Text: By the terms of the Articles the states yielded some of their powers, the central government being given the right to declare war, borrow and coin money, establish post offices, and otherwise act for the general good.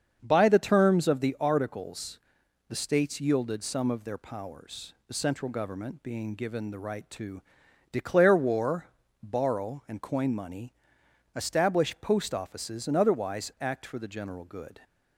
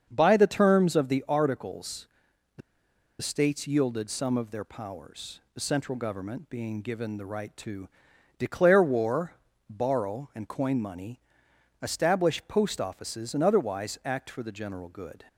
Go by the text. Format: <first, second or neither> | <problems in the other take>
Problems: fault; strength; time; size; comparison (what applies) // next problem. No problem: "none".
first | starts louder than the rest; until 1.1 s; 7 dB; also in the first // pauses between "Articles" and "the"; noticeable; at 2.0 s; 0.48 s long; noticeable in the first // pauses between "the" and "states"; noticeable; at 2.6 s; 0.61 s long // pauses between "to" and "declare"; noticeable; at 7.8 s; 0.48 s long; noticeable in the first